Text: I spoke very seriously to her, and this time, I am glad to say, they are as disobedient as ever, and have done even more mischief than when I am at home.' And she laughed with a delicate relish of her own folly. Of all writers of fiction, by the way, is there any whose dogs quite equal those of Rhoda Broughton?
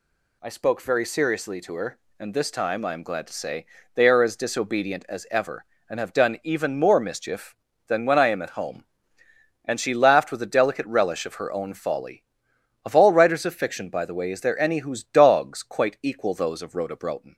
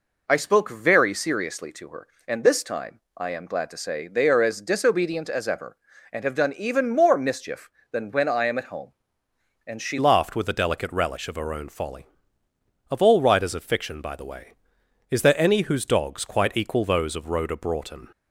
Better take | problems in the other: first | changes voice at "laughed"; from 9.9 s on; 8.1 s long

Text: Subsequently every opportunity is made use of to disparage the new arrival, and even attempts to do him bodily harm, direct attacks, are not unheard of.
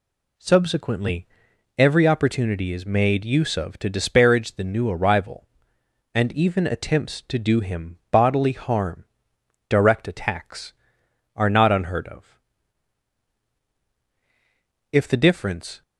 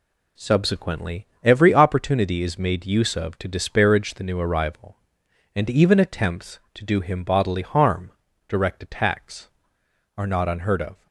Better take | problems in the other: second | pauses between "Subsequently" and "every"; noticeable; at 1.2 s; 0.52 s long; slight in the second // goes on to say "If the difference"; noticeable; from 14.9 s on; 0.90 s long

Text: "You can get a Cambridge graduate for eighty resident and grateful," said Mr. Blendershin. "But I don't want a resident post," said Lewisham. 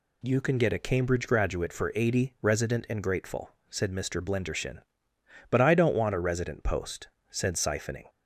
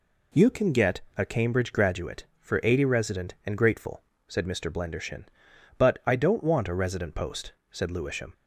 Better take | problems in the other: second | says "Siphoning" for "Lewisham"; at 7.5 s

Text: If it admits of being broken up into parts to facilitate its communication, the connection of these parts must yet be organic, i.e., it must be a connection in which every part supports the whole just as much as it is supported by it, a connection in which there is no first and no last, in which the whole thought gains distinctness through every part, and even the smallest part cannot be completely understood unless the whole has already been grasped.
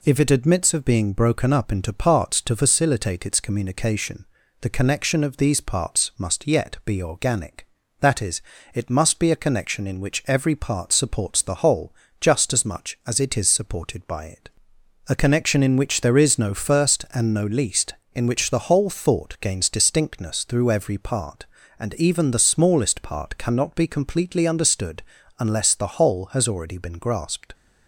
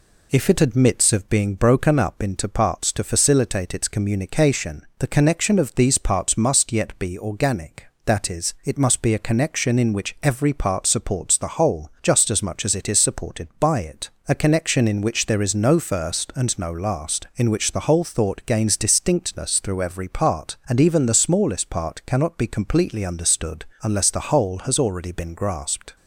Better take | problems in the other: second | pauses between "whole" and "just"; slight; at 11.9 s; 0.26 s long // says "least" for "last"; at 17.4 s // pauses between "understood" and "unless"; slight; at 25.0 s; 0.36 s long; slight in the second

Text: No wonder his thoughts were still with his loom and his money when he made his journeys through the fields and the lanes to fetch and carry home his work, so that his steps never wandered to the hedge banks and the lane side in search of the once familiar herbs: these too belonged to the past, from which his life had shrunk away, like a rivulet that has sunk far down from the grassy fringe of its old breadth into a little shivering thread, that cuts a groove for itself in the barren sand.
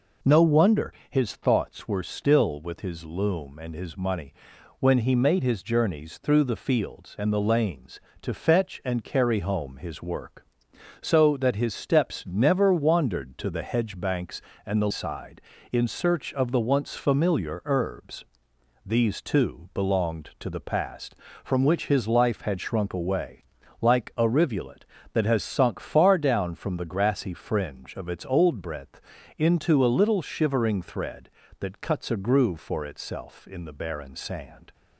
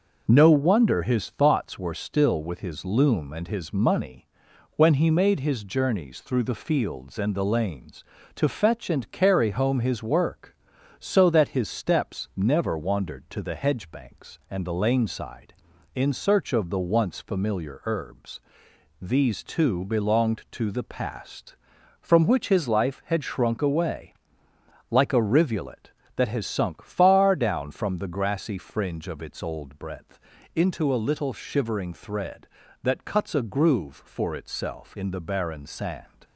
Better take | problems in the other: second | pauses between "wonder" and "his"; slight; at 0.9 s; 0.16 s long // pauses between "money" and "when"; at 4.3 s; 0.44 s long; noticeable in the second // skips "lane"; at 14.8 s // pauses between "breadth" and "into"; at 29.0 s; 0.38 s long; slight in the second

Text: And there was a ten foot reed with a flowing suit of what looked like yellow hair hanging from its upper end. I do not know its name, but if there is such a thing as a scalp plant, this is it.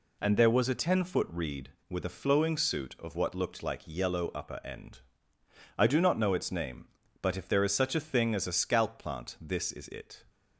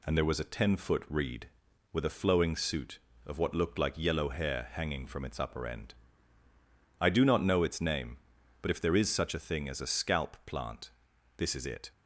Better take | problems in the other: second | skips "hair hanging from its"; at 4.3 s

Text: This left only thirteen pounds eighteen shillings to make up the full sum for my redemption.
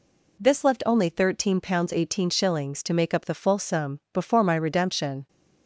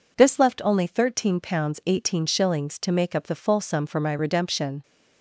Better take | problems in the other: second | says "before" for "for"; at 4.1 s

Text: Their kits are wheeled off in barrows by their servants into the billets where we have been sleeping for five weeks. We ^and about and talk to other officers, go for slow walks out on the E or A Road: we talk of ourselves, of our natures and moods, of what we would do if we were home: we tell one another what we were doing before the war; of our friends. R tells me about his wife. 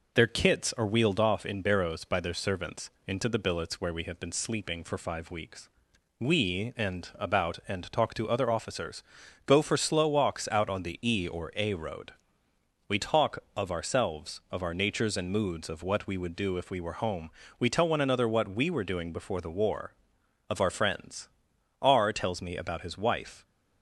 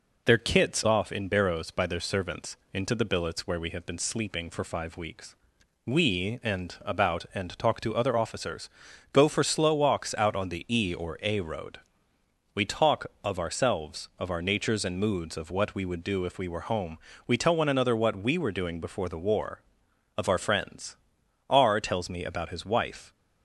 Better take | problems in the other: first | skips "are wheeled"; at 0.8 s // pauses between "servants" and "into"; slight; at 2.5 s; 0.16 s long; slight in the first

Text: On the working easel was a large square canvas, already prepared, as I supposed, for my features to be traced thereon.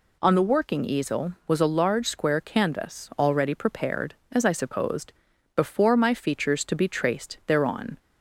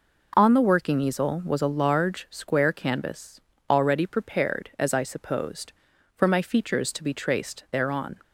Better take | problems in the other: second | says "before" for "for"; at 5.5 s

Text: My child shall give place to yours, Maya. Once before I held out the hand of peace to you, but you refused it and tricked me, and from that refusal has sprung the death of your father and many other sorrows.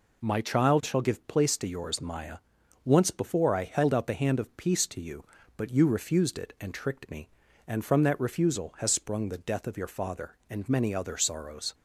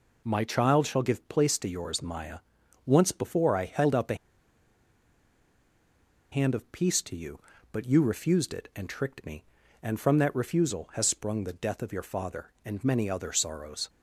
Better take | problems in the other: first | pauses between "the" and "hand"; strong; at 4.1 s; 2.1 s long

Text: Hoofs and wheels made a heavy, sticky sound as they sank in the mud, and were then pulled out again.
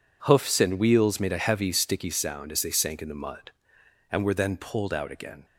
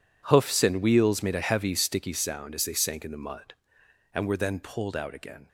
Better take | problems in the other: first | gets quieter; strong; throughout; 16.5 dB

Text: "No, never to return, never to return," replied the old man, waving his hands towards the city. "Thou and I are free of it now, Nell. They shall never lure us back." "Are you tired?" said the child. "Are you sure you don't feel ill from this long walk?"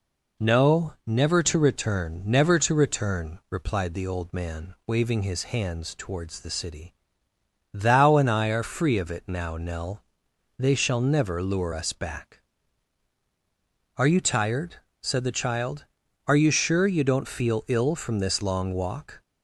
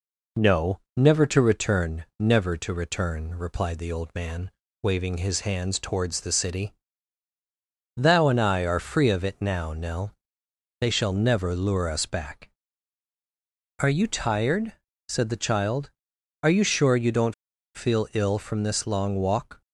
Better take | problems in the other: first | pauses between "don't" and "feel"; at 17.3 s; 0.40 s long

